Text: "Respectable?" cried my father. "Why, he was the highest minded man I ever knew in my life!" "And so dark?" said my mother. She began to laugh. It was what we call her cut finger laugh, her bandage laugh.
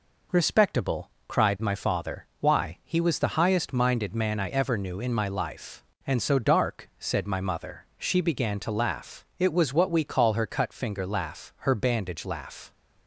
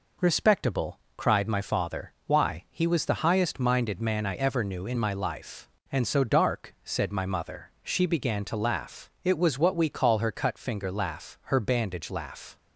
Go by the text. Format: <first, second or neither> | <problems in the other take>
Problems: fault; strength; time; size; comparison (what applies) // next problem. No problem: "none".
neither | none